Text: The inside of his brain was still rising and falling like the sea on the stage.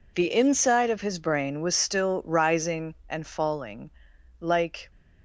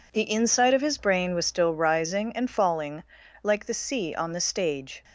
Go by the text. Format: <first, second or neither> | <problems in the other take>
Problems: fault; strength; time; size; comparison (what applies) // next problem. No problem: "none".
second | pauses between "falling" and "like"; noticeable; at 3.8 s; 0.52 s long; also in the second // stops before "the sea on the stage"; at 4.9 s